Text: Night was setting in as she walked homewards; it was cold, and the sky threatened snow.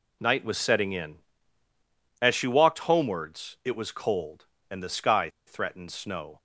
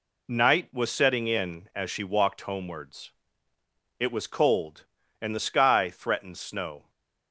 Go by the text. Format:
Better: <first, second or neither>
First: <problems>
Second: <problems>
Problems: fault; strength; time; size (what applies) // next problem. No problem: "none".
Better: second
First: pauses between "sky" and "threatened"; slight; at 5.2 s; 0.18 s long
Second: none